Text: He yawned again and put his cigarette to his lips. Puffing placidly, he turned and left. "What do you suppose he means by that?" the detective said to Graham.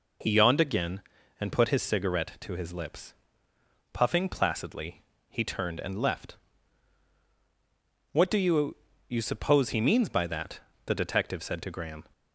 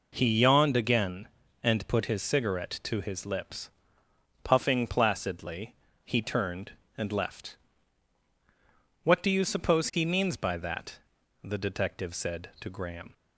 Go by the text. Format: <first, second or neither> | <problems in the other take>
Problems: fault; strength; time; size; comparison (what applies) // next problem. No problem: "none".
second | says "you" twice; at 9.0 s